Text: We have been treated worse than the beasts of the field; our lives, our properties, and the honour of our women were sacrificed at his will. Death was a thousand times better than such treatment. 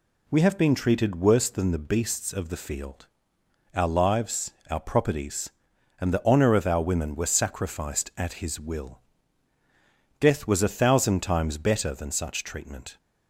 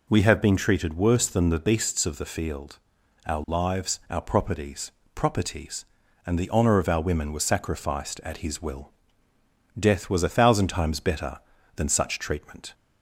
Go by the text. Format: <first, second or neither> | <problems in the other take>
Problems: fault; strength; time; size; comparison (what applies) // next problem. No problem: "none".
first | says "properties" twice; at 5.1 s